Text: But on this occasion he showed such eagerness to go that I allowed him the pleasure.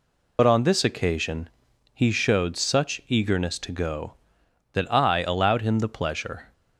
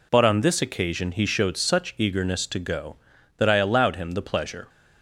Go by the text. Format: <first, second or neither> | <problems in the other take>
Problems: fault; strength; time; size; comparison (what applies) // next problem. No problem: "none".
second | loses the start of "But"; at 0.3 s; 70 ms // pauses between "occasion" and "he"; at 1.4 s; 0.44 s long